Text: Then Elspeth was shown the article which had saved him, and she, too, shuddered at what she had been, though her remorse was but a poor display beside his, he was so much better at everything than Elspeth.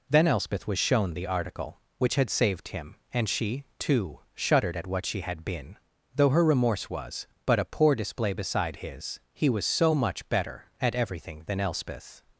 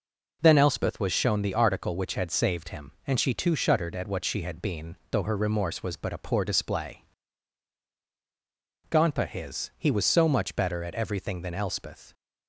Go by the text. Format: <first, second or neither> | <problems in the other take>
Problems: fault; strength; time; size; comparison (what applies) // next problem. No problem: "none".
first | says "gonpa" for "beside"; at 8.8 s